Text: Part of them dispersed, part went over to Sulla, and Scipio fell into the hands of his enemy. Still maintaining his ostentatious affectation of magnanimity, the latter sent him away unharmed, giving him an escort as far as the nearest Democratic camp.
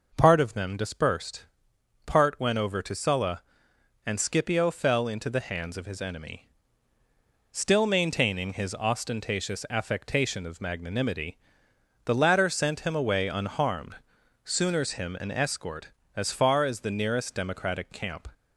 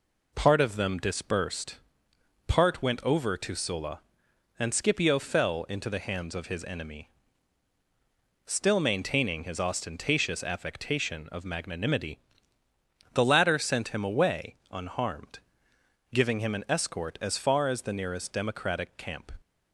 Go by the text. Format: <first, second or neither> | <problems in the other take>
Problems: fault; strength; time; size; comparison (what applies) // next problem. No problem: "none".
second | says "sooners" for "giving"; at 14.4 s